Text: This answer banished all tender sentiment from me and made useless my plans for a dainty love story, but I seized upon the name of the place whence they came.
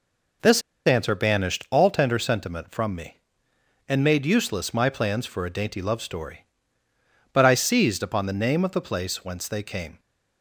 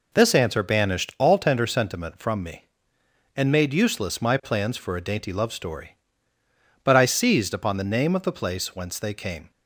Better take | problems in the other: second | pauses between "This" and "answer"; slight; at 0.6 s; 0.25 s long

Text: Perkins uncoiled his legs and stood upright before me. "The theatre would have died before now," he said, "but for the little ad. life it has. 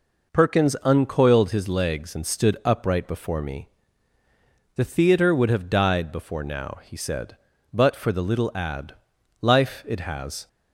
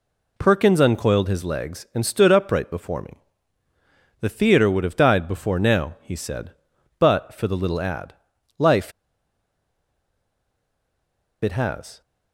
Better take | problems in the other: first | pauses between "life" and "it"; strong; at 8.9 s; 2.5 s long

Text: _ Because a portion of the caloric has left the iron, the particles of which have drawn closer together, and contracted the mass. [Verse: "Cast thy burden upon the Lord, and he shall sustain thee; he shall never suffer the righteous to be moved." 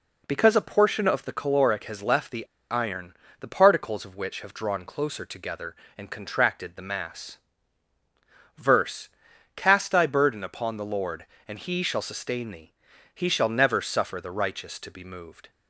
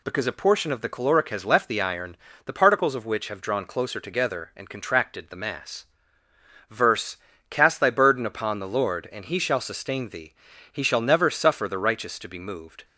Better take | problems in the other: second | pauses between "the" and "iron"; slight; at 2.4 s; 0.24 s long

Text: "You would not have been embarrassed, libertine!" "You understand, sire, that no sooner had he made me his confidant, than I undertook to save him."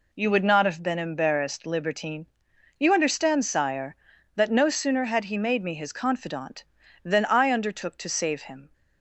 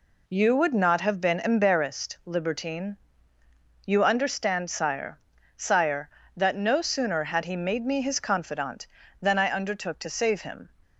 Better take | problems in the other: first | says "sire" twice; at 5.5 s

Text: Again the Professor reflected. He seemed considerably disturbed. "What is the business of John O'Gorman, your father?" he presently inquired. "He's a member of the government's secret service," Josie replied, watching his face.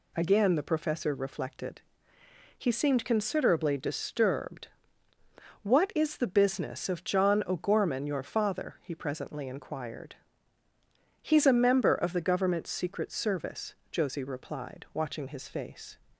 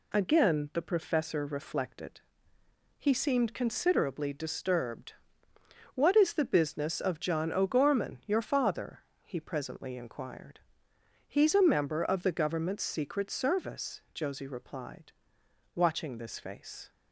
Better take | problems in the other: first | says "this" for "his"; at 16.1 s

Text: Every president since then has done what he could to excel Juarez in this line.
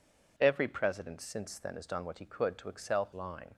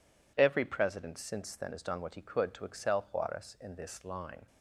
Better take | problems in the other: second | skips "Juarez in this"; at 3.1 s

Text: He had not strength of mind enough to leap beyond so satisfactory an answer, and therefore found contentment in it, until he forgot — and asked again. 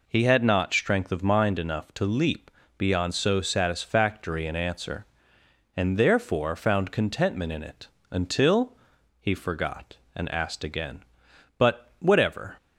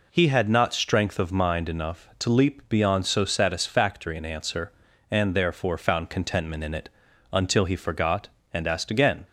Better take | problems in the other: second | pauses between "leap" and "beyond"; slight; at 2.5 s; 0.26 s long // pauses between "until" and "he"; at 8.7 s; 0.42 s long // goes on to say "But whatever"; noticeable; from 11.5 s on; 1.0 s long

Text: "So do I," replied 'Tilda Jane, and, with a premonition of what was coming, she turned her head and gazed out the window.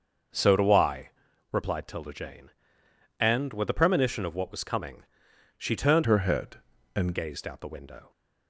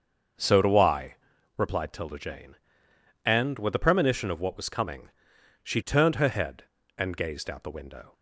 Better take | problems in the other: second | starts louder than the rest; until 1.7 s; 6 dB; also in the second // changes voice from "her" to "and"; from 6.0 to 7.1 s; 1.1 s long

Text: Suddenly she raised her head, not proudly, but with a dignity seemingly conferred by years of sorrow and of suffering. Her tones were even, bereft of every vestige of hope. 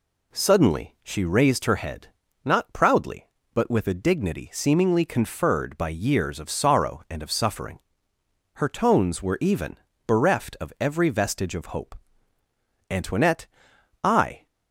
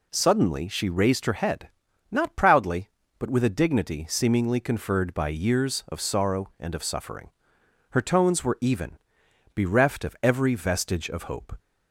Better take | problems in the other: second | goes on to say "Antoinette I"; from 12.8 s on; 1.5 s long

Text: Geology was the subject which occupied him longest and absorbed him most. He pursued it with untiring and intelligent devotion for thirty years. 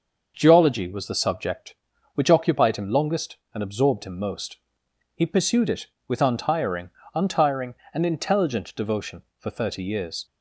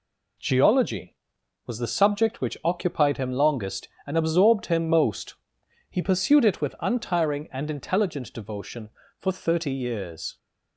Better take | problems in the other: second | starts louder than the rest; until 1.3 s; 6.5 dB // says "untiring" twice; at 7.1 s

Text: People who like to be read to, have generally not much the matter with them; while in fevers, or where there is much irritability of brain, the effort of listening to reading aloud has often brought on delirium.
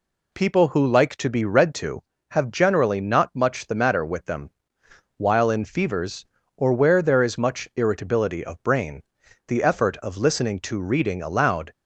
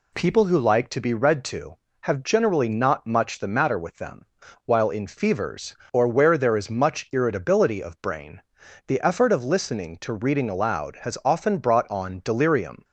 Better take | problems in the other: second | stops before "has often brought on delirium"; at 11.7 s

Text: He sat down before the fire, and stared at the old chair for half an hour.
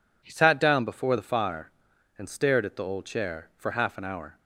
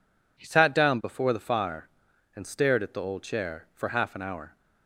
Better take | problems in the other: neither | none

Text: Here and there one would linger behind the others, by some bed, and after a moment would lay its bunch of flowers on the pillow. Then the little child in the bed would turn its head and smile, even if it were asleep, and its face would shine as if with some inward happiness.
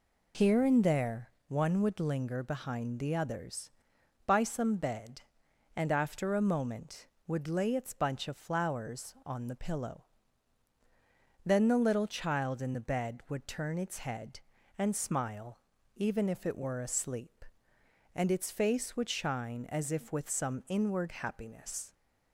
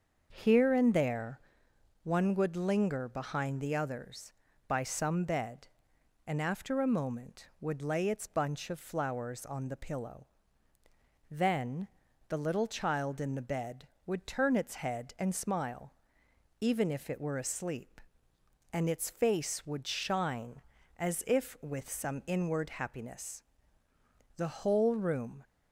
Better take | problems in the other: first | starts louder than the rest; until 1.3 s; 6.5 dB // pauses between "there" and "one"; noticeable; at 1.3 s; 0.64 s long; slight in the first // pauses between "Then" and "the"; at 11.8 s; 0.42 s long // goes on to say "The whole room"; noticeable; from 24.3 s on; 1.0 s long

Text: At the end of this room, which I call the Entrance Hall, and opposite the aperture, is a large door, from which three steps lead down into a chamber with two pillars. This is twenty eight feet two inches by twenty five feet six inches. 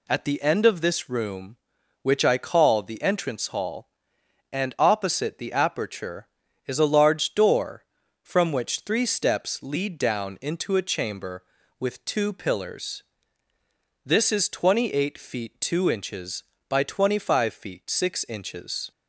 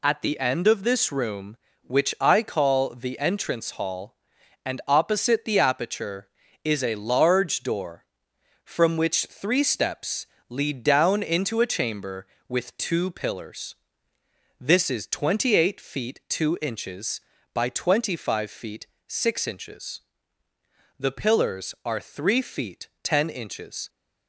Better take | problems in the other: first | pauses between "steps" and "lead"; slight; at 10.2 s; 0.22 s long // pauses between "feet" and "six"; slight; at 18.8 s; 0.20 s long // goes on to say "The pillars are three feet ten inches"; strong; from 20.9 s on; 2.9 s long

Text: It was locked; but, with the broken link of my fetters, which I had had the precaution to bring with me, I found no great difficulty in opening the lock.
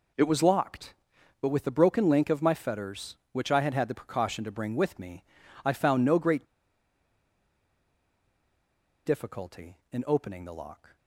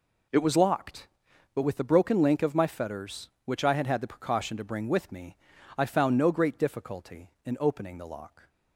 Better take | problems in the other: second | pauses between "great" and "difficulty"; strong; at 6.4 s; 2.6 s long

